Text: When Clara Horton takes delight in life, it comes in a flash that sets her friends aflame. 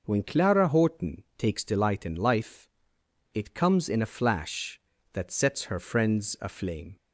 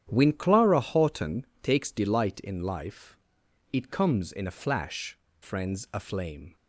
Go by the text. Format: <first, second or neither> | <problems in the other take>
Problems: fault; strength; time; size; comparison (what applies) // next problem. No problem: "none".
first | starts louder than the rest; strong; until 1.1 s; 10 dB // pauses between "Horton" and "takes"; slight; at 1.4 s; 0.16 s long // skips "that sets her"; at 5.2 s